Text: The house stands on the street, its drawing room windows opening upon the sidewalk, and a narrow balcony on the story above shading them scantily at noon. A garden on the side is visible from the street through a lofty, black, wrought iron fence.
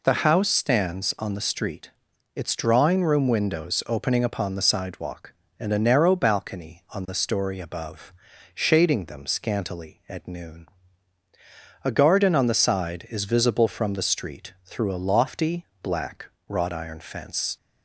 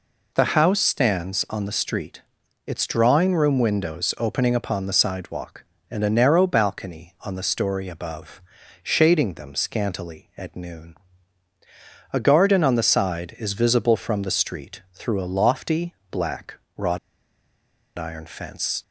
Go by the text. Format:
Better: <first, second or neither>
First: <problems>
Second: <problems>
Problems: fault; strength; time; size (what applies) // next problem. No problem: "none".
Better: first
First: pauses between "above" and "shading"; at 8.1 s; 0.42 s long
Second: pauses between "above" and "shading"; at 8.4 s; 0.42 s long // pauses between "wrought" and "iron"; at 16.9 s; 0.99 s long